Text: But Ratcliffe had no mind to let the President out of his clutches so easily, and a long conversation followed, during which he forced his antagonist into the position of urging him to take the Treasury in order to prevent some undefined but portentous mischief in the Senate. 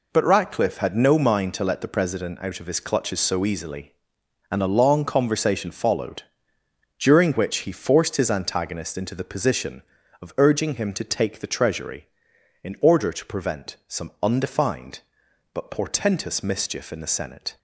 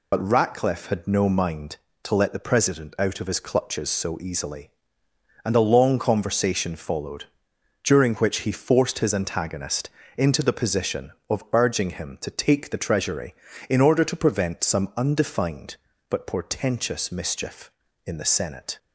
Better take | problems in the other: first | loses the start of "But"; at 0.1 s; 45 ms // pauses between "antagonist" and "into"; slight; at 9.8 s; 0.26 s long

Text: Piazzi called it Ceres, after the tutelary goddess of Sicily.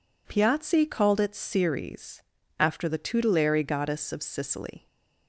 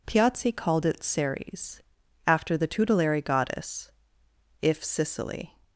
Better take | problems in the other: first | says "if" for "of"; at 4.6 s

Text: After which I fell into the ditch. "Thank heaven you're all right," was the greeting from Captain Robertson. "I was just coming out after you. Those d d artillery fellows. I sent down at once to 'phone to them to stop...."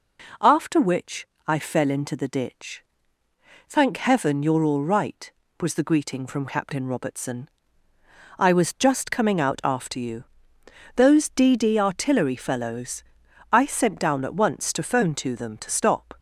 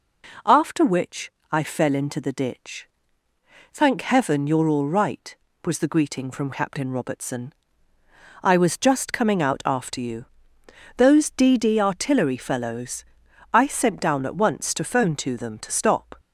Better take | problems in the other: neither | pauses between "which" and "I"; slight; the same in both

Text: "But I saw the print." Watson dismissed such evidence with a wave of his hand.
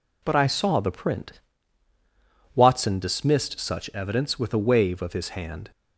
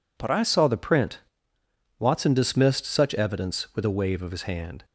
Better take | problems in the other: neither | none

